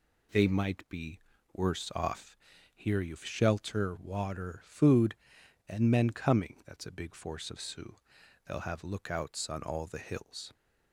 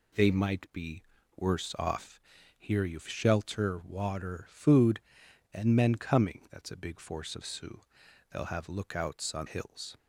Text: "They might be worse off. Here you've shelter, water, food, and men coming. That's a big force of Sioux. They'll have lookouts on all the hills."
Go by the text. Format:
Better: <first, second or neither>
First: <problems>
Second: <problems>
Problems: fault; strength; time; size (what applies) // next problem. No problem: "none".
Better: first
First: pauses between "be" and "worse"; slight; at 1.1 s; 0.34 s long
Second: pauses between "be" and "worse"; slight; at 1.0 s; 0.34 s long // skips "all the"; at 9.4 s